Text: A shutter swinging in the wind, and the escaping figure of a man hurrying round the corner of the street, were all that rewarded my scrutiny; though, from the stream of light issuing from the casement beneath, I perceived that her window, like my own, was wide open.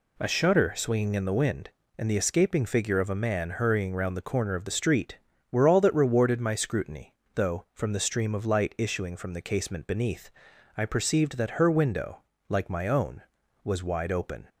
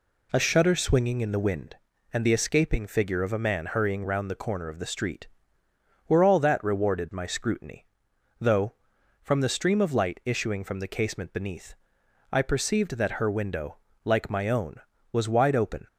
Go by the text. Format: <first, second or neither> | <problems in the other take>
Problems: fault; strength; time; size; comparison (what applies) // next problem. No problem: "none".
neither | none